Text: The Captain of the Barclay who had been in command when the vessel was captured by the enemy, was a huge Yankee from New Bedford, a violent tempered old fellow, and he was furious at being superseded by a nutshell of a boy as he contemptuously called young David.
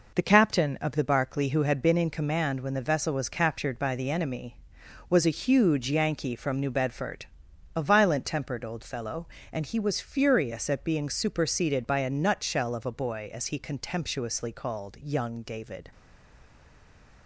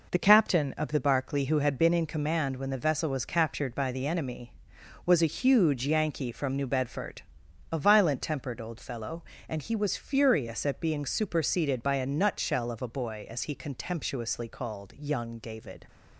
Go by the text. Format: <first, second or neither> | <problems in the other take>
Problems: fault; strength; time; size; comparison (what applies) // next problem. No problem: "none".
second | stays silent after the last word; noticeable; from 15.9 s on; 1.3 s long